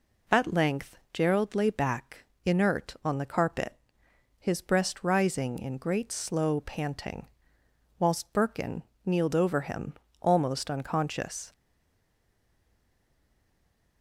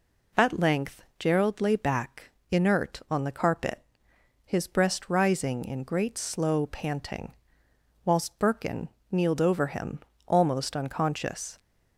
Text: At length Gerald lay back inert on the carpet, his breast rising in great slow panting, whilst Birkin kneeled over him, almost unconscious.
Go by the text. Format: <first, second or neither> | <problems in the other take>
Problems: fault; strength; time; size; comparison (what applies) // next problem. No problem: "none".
second | pauses between "length" and "Gerald"; slight; at 0.9 s; 0.18 s long; slight in the second // pauses between "back" and "inert"; slight; at 2.2 s; 0.20 s long; slight in the second // pauses between "Birkin" and "kneeled"; slight; at 8.8 s; 0.24 s long; slight in the second // stays silent after the last word; from 11.5 s on; 2.5 s long